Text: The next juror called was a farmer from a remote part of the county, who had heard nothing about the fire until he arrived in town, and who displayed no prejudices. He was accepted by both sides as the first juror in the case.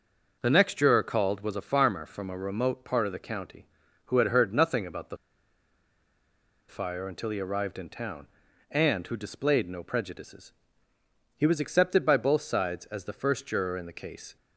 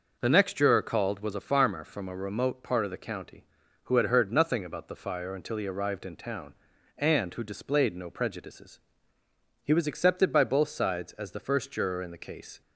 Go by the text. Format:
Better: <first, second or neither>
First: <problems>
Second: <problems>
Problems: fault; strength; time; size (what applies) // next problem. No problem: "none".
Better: second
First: pauses between "the" and "fire"; strong; at 5.1 s; 1.5 s long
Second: none